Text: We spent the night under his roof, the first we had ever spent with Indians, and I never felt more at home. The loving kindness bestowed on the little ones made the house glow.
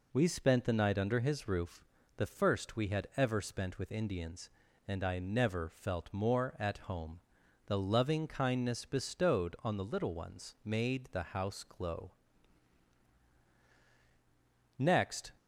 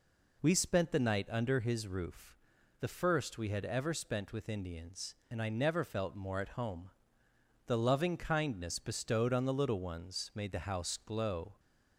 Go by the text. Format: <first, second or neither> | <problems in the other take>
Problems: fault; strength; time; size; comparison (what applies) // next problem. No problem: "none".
second | goes on to say "Next"; from 14.7 s on; 0.54 s long